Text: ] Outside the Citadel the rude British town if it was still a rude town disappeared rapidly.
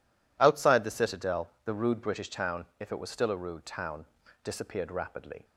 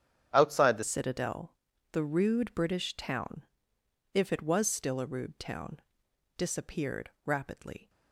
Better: first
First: pauses between "town" and "disappeared"; slight; at 4.0 s; 0.36 s long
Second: starts louder than the rest; strong; until 1.3 s; 9 dB // changes voice at "Citadel"; from 0.8 s on; 7.0 s long // pauses between "Citadel" and "the"; slight; at 1.5 s; 0.36 s long // pauses between "town" and "if"; noticeable; at 3.4 s; 0.70 s long // pauses between "town" and "disappeared"; noticeable; at 5.8 s; 0.56 s long // pauses between "disappeared" and "rapidly"; slight; at 7.0 s; 0.16 s long

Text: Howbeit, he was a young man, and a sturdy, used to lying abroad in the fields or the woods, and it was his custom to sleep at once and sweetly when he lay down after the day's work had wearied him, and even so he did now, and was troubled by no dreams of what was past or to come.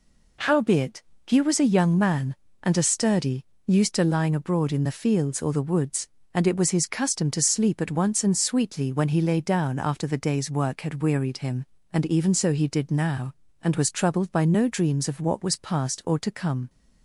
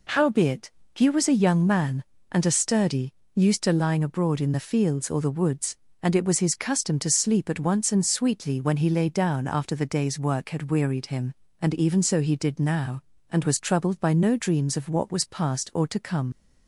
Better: first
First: none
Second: leaves "come" unfinished; at 16.3 s; 55 ms

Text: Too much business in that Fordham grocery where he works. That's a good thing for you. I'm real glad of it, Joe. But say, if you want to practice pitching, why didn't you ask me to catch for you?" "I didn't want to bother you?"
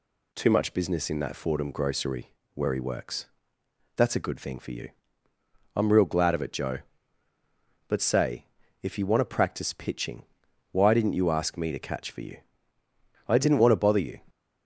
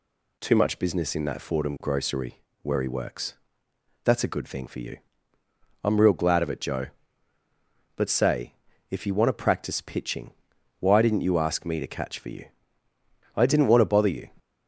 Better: neither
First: pauses between "grocery" and "where"; slight; at 2.3 s; 0.22 s long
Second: pauses between "grocery" and "where"; slight; at 2.4 s; 0.22 s long

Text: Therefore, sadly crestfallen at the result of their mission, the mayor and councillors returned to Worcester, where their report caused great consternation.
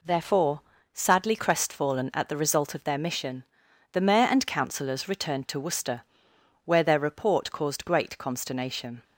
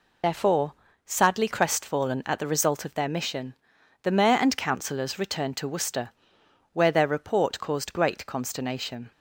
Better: first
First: none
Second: loses the start of "Therefore"; at 0.2 s; 85 ms

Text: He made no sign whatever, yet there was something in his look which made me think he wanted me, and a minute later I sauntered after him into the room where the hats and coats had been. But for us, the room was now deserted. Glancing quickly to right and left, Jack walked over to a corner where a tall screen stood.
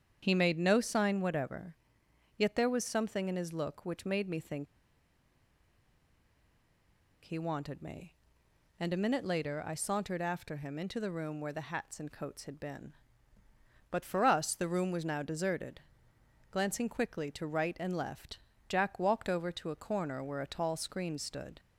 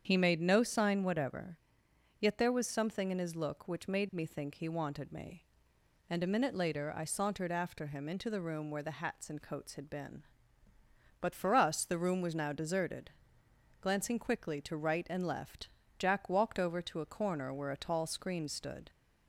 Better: second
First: starts louder than the rest; strong; until 1.2 s; 8 dB // pauses between "think" and "he"; strong; at 4.6 s; 2.5 s long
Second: starts louder than the rest; strong; until 1.0 s; 8 dB

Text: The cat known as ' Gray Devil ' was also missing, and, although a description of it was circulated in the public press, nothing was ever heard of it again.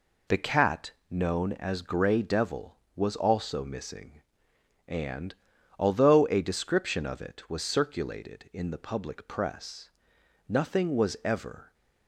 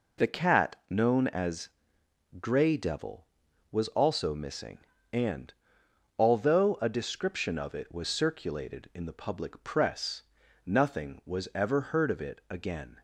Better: second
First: pauses between "cat" and "known"; slight; at 0.9 s; 0.16 s long // stops before "heard of it again"; at 11.7 s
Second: none

